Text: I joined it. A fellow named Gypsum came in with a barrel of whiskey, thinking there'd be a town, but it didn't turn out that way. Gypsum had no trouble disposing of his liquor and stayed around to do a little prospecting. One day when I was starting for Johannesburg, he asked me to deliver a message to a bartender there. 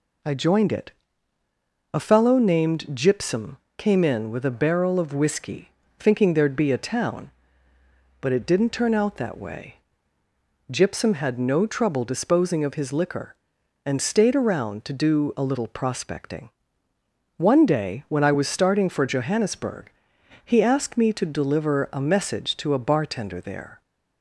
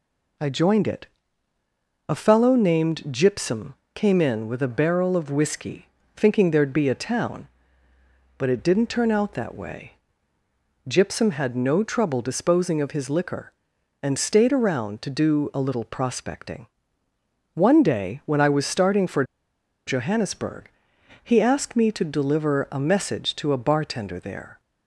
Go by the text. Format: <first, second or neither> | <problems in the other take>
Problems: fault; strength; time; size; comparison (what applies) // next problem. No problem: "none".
first | pauses between "Gypsum" and "came"; slight; at 3.7 s; 0.22 s long; slight in the first // pauses between "for" and "Johannesburg"; noticeable; at 19.2 s; 0.63 s long